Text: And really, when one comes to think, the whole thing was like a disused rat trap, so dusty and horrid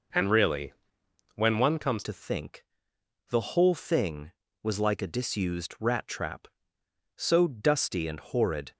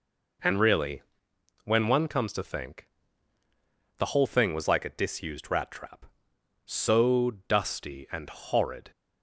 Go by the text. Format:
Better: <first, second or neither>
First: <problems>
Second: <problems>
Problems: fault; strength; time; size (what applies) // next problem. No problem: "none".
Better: second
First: changes voice at "to"; from 2.0 s on; 6.7 s long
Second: none